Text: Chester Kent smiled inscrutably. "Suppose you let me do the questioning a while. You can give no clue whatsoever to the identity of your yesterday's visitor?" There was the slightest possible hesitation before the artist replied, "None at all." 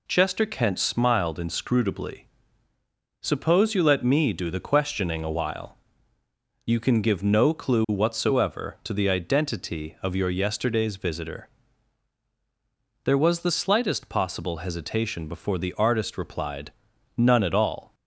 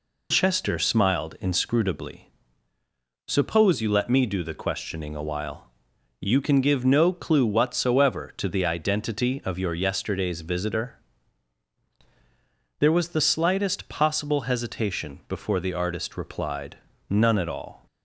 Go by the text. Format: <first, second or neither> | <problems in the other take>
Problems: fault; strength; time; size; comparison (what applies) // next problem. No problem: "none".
first | skips "Kent"; at 0.7 s